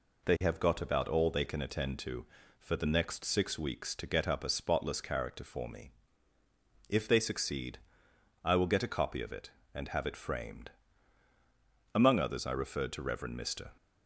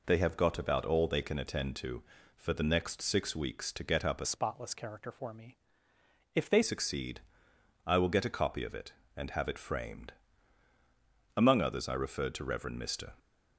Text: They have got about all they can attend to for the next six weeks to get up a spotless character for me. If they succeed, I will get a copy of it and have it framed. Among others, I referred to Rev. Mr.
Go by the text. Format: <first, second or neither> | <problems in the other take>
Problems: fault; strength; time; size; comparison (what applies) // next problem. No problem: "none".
first | changes voice from "spotless" to "they"; from 4.2 to 6.6 s; 2.4 s long